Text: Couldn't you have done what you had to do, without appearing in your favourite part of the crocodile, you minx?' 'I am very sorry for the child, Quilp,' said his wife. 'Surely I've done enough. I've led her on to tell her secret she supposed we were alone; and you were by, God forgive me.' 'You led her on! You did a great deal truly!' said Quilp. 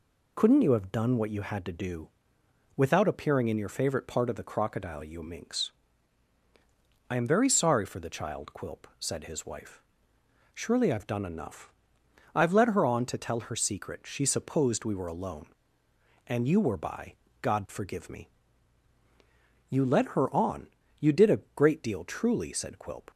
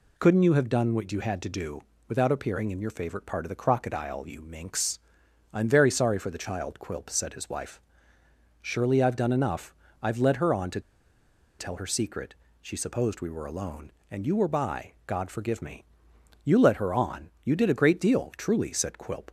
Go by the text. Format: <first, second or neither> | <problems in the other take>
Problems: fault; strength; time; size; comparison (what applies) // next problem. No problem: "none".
first | pauses between "to" and "tell"; noticeable; at 10.8 s; 0.78 s long // pauses between "secret" and "she"; slight; at 12.3 s; 0.26 s long